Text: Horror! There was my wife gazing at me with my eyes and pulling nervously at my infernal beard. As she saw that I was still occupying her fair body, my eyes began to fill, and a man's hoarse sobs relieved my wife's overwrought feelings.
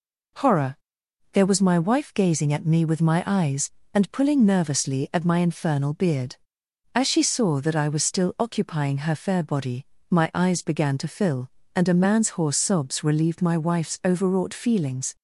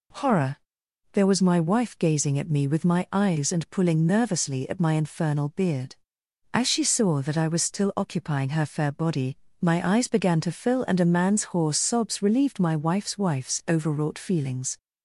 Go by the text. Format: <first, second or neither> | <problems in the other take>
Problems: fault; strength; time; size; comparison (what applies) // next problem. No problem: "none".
first | says "wife's" twice; at 13.1 s